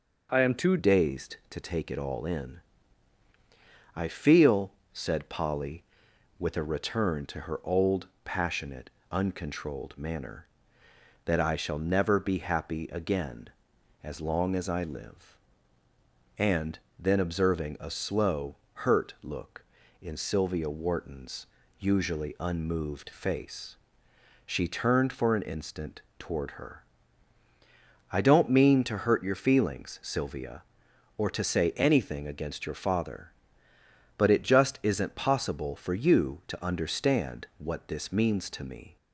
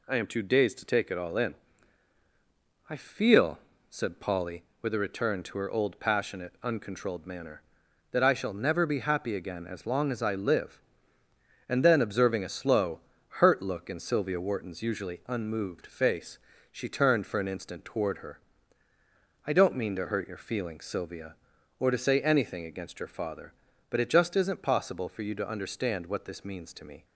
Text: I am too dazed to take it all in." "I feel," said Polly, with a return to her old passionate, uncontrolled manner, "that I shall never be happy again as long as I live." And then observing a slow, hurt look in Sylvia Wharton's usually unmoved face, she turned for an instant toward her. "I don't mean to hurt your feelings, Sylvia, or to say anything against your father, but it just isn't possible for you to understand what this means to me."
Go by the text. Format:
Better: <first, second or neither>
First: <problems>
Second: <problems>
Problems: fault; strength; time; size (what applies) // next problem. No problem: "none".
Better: second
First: changes voice at "dazed"; from 0.7 s on; 38.2 s long // pauses between "old" and "passionate"; slight; at 8.0 s; 0.16 s long // pauses between "And" and "then"; slight; at 16.7 s; 0.20 s long // pauses between "Wharton's" and "usually"; slight; at 21.4 s; 0.32 s long // pauses between "instant" and "toward"; slight; at 26.0 s; 0.18 s long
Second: none